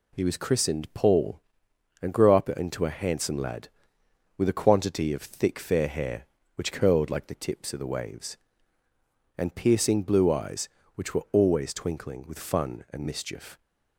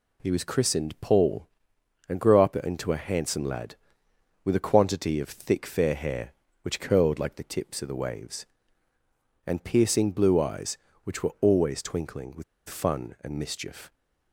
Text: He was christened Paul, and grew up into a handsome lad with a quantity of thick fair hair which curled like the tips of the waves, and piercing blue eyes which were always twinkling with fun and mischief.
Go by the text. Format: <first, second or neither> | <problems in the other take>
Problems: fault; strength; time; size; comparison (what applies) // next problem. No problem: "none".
first | pauses between "with" and "fun"; slight; at 12.4 s; 0.25 s long